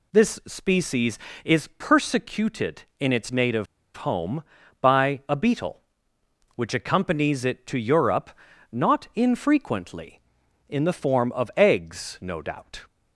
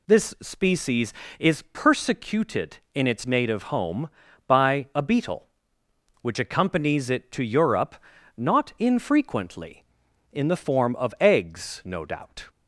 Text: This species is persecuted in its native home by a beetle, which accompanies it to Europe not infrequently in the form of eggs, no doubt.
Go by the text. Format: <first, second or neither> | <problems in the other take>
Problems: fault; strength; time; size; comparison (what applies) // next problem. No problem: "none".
second | pauses between "native" and "home"; slight; at 3.6 s; 0.31 s long // pauses between "Europe" and "not"; at 8.3 s; 0.40 s long; also in the second